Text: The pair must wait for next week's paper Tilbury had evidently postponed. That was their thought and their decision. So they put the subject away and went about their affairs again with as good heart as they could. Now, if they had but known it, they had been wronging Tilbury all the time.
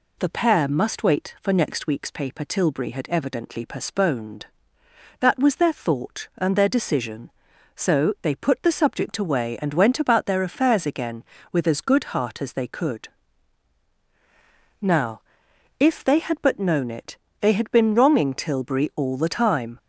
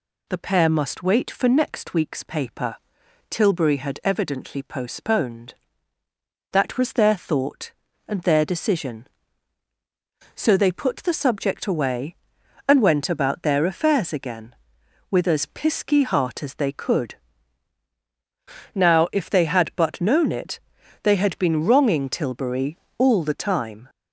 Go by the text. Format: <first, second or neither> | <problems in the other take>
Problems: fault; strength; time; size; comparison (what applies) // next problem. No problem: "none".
first | pauses between "paper" and "Tilbury"; noticeable; at 2.7 s; 0.52 s long // says "pisky" for "good"; at 15.4 s // pauses between "Tilbury" and "all"; slight; at 22.7 s; 0.20 s long